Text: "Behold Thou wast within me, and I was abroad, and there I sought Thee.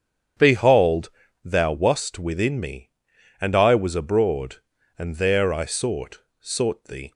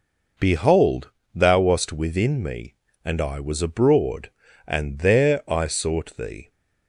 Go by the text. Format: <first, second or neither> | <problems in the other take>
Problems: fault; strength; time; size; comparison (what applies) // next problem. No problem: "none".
second | starts louder than the rest; strong; until 1.7 s; 8.5 dB // pauses between "Behold" and "Thou"; slight; at 1.0 s; 0.34 s long; slight in the second // says "sought" twice; at 6.3 s